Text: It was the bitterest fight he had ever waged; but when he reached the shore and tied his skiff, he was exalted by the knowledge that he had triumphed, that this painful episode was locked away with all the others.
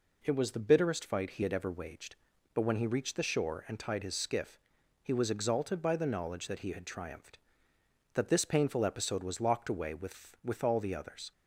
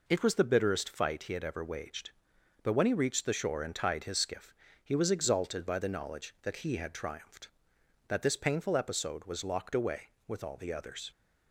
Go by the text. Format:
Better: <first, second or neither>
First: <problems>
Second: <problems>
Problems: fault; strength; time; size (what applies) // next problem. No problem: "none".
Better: second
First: says "with" twice; at 10.4 s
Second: none